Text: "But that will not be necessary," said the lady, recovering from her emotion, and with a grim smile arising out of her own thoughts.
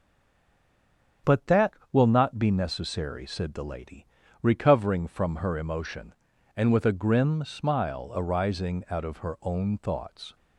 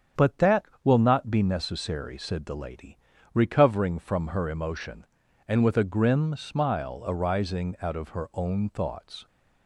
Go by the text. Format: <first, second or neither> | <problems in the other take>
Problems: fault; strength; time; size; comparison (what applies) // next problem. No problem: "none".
second | stays silent before the first word; noticeable; until 1.2 s; 1.2 s long // starts louder than the rest; strong; until 2.4 s; 8 dB; strong in the second